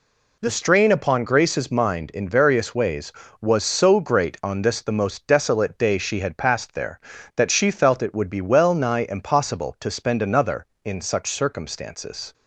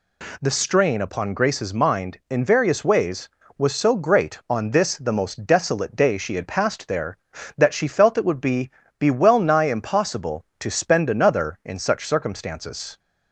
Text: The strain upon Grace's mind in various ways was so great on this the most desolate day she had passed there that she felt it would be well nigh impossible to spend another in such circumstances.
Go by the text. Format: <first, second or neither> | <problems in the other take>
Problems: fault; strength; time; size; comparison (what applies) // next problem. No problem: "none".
first | says "be" twice; at 8.9 s